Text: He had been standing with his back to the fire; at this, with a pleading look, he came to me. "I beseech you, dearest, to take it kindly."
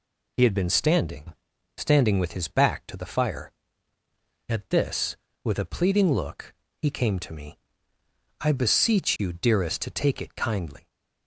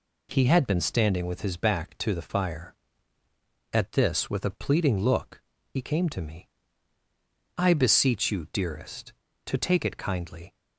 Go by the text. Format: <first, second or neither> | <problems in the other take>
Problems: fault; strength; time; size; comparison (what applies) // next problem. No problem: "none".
second | says "standing" twice; at 1.7 s